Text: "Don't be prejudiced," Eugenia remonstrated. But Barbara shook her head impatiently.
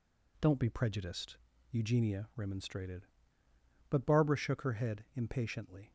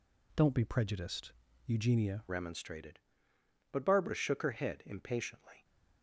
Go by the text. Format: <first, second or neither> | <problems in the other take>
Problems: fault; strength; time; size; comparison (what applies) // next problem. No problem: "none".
first | changes voice at "remonstrated"; from 2.2 s on; 3.4 s long